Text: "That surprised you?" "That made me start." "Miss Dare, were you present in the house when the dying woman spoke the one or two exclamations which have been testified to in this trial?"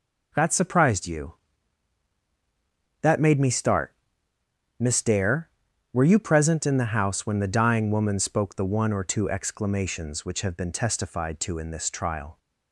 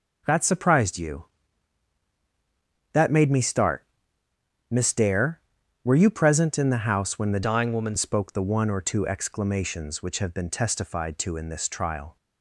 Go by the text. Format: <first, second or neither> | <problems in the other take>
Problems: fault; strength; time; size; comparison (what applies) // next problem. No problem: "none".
first | changes voice from "dying" to "woman"; from 7.4 to 7.9 s; 0.5 s long